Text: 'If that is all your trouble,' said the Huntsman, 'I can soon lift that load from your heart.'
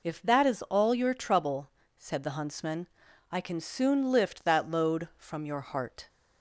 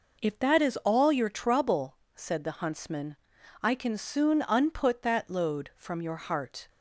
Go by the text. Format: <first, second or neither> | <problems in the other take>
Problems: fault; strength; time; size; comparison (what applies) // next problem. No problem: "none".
first | says "unput" for "lift"; at 4.4 s